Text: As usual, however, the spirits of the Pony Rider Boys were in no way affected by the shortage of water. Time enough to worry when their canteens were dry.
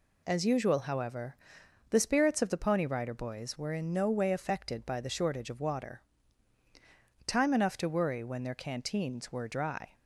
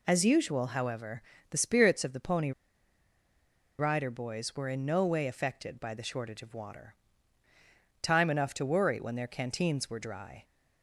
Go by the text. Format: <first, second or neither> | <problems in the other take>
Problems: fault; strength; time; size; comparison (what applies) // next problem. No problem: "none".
first | pauses between "Pony" and "Rider"; strong; at 2.5 s; 1.2 s long